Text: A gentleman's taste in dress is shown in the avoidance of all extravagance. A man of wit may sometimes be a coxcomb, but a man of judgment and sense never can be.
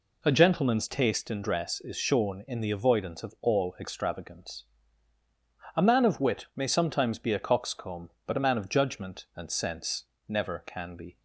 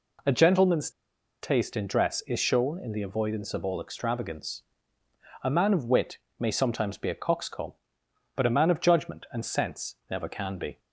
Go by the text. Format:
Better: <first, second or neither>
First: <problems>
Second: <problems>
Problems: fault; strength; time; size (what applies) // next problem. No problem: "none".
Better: first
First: pauses between "sense" and "never"; slight; at 10.0 s; 0.24 s long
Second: pauses between "gentleman's" and "taste"; noticeable; at 0.8 s; 0.52 s long // pauses between "wit" and "may"; slight; at 6.1 s; 0.20 s long // pauses between "sense" and "never"; slight; at 9.9 s; 0.16 s long